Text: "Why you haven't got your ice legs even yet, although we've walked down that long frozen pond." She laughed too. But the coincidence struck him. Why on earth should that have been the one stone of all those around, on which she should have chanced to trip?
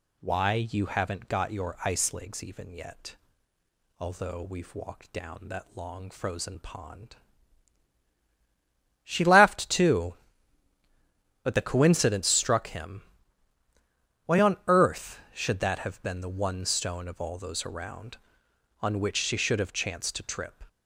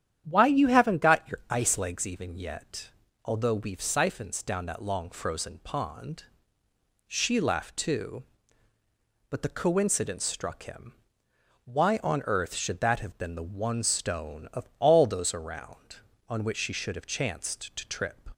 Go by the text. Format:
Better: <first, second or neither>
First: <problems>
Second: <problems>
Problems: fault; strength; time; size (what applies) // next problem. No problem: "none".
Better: first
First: none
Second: starts louder than the rest; strong; until 1.2 s; 10 dB // says "siphons" for "walked"; at 3.8 s